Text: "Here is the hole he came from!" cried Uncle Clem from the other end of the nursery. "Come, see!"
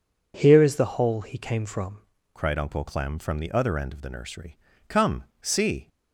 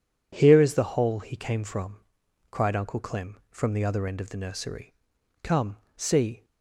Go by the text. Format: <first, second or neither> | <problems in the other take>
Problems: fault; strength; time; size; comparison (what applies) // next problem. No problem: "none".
second | changes voice at "cried"; from 2.3 s on; 3.5 s long